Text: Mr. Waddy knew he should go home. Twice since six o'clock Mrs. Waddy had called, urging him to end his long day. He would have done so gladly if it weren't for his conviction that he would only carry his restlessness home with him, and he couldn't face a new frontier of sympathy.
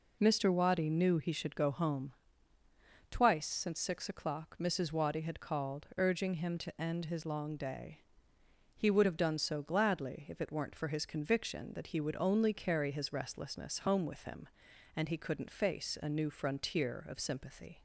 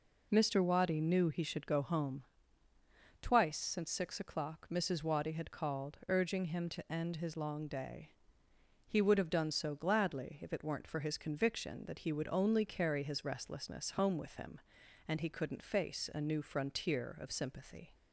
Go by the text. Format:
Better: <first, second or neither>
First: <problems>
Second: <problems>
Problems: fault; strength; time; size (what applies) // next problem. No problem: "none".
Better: neither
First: none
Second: none